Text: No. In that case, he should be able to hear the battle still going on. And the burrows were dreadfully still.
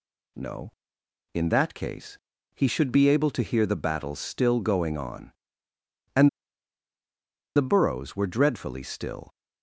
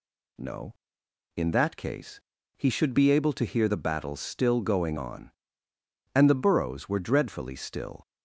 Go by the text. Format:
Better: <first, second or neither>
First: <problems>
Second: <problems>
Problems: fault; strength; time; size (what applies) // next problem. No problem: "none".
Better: second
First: pauses between "And" and "the"; strong; at 6.2 s; 1.2 s long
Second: none